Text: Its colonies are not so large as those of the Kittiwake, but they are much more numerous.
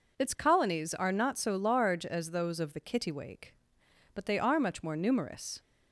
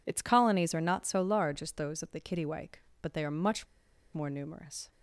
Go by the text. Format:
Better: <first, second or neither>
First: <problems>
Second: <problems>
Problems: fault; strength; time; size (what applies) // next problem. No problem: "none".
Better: first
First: none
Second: pauses between "much" and "more"; noticeable; at 3.6 s; 0.47 s long